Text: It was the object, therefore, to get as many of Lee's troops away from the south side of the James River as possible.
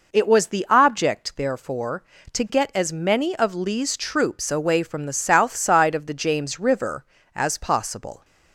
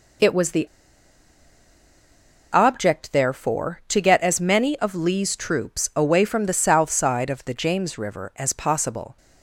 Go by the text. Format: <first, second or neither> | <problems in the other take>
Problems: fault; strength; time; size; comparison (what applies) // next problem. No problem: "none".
first | pauses between "the" and "object"; strong; at 0.6 s; 1.8 s long